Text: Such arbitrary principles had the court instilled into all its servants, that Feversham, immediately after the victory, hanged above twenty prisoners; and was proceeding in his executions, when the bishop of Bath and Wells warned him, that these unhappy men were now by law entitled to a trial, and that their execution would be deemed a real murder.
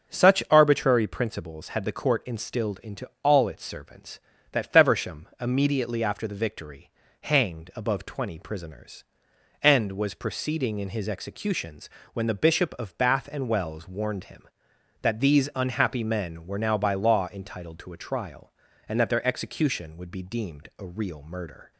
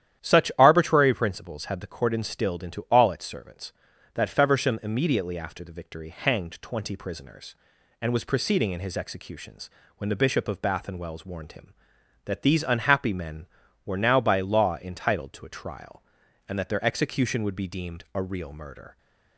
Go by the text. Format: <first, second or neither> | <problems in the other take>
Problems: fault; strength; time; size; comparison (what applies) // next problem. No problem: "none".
first | starts louder than the rest; strong; until 1.2 s; 11 dB; also in the first // skips "above"; at 6.6 s